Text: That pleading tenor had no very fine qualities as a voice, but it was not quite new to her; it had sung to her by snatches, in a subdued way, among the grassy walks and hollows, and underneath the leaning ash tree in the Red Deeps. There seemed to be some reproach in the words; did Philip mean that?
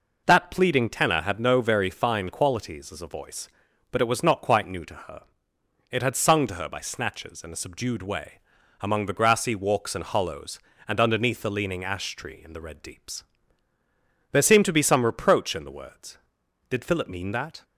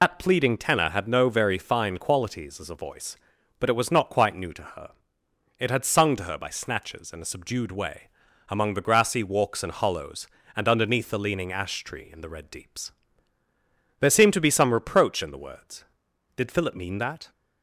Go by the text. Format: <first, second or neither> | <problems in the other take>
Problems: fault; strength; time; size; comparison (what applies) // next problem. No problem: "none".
first | loses the start of "That"; at 0.0 s; 80 ms